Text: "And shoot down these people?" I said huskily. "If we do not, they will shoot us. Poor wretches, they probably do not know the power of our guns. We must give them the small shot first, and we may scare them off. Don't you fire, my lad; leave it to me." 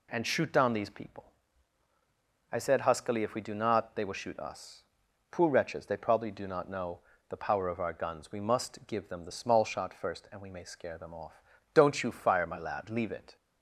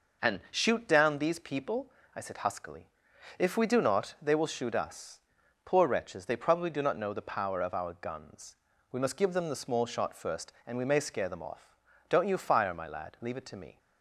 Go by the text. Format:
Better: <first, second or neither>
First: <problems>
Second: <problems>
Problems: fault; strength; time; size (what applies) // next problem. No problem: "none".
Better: second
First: pauses between "know" and "the"; slight; at 7.0 s; 0.28 s long // stops before "to me"; at 13.3 s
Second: none